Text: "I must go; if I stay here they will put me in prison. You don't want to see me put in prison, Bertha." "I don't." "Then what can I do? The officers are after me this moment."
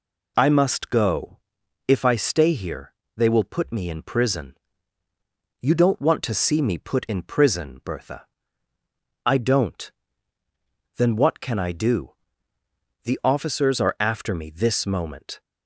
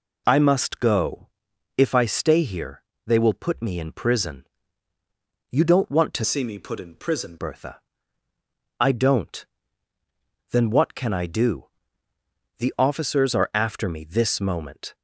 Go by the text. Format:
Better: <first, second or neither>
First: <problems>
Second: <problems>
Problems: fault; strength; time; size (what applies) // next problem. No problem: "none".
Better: first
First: pauses between "here" and "they"; slight; at 2.9 s; 0.22 s long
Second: pauses between "here" and "they"; slight; at 2.8 s; 0.22 s long // changes voice from "see" to "prison"; from 6.2 to 7.3 s; 1.1 s long